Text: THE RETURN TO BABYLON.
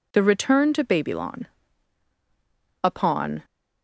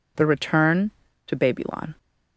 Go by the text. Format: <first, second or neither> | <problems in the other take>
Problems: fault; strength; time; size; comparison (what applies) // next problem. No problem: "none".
second | goes on to say "Upon"; noticeable; from 2.8 s on; 0.62 s long